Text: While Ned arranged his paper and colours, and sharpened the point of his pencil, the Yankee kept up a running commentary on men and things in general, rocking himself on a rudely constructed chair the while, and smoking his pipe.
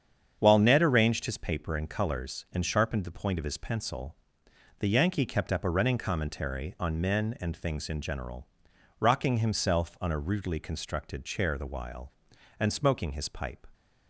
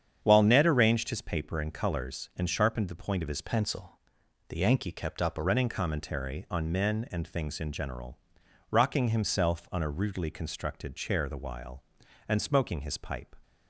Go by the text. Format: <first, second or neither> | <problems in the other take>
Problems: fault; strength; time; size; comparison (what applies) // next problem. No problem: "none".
first | starts louder than the rest; strong; until 1.2 s; 8 dB; strong in the first // changes voice from "pencil" to "a"; from 3.4 to 5.4 s; 2.0 s long